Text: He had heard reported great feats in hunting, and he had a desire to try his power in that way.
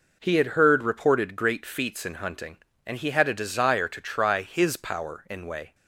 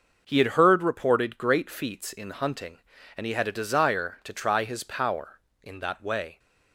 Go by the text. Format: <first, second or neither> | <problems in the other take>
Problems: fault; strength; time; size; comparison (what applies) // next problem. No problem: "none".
second | skips "that"; at 5.4 s